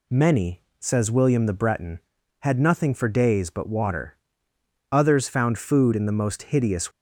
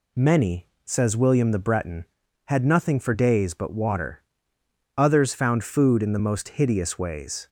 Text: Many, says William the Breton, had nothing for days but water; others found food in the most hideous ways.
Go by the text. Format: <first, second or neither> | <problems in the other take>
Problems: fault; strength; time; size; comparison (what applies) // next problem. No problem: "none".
second | stops before "ways"; at 6.9 s